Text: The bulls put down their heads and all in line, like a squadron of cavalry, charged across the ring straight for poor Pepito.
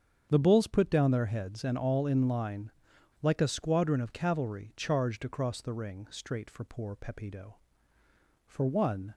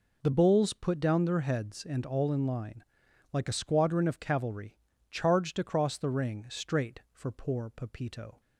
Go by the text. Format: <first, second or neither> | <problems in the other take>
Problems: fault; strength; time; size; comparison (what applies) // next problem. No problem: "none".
second | starts louder than the rest; strong; until 1.3 s; 7.5 dB // goes on to say "For one"; noticeable; from 8.4 s on; 0.68 s long